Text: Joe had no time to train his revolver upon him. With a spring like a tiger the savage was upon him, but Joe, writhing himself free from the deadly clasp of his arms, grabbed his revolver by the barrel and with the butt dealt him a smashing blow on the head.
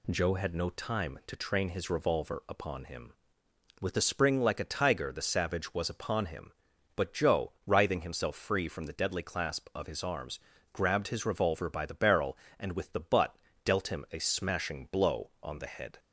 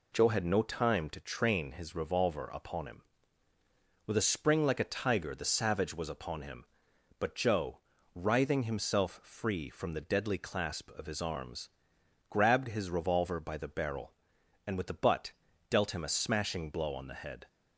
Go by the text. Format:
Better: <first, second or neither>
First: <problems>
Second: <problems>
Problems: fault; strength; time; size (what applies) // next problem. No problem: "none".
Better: neither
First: pauses between "butt" and "dealt"; slight; at 13.3 s; 0.28 s long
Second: pauses between "butt" and "dealt"; at 15.3 s; 0.38 s long